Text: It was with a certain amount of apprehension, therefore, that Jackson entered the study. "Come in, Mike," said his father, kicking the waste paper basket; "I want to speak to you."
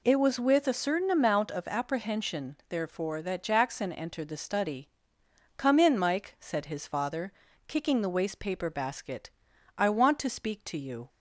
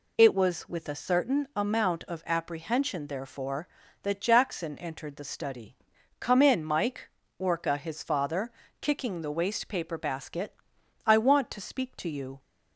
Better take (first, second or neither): first